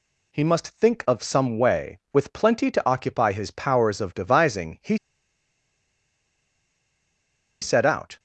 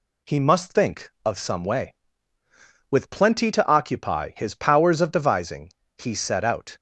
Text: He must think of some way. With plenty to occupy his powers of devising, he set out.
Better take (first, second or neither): second